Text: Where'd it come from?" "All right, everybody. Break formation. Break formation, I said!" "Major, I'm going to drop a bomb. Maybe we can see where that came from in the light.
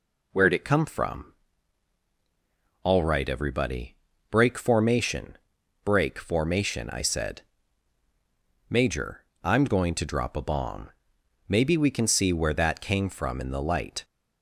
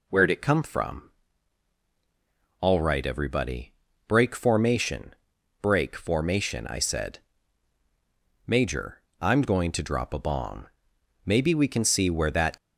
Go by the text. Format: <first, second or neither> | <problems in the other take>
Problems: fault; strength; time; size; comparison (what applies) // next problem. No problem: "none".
first | stops before "came from in the light"; at 12.5 s